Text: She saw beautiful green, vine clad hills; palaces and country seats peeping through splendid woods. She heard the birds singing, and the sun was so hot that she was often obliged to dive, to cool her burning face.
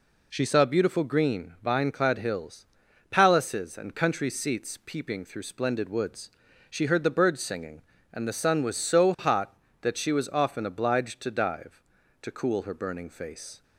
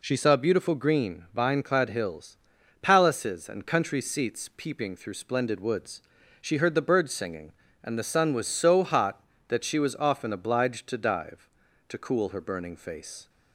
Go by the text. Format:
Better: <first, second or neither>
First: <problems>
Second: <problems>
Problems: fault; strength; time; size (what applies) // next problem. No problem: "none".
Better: neither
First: none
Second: none